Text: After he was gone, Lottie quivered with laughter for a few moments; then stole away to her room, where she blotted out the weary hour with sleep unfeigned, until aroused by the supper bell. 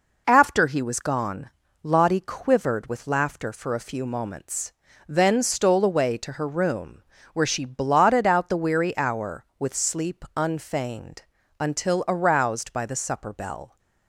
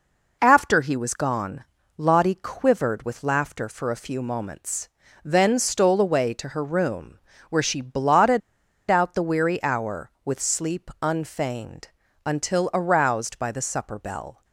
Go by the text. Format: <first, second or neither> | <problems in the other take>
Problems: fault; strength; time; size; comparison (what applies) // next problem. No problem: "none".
first | pauses between "blotted" and "out"; noticeable; at 8.4 s; 0.48 s long